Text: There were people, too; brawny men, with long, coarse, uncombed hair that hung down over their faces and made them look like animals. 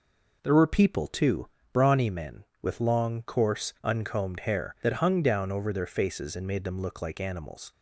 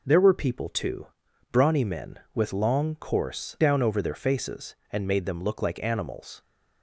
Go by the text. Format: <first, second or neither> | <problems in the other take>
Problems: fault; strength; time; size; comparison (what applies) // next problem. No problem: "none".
first | skips "uncombed hair that hung"; at 3.5 s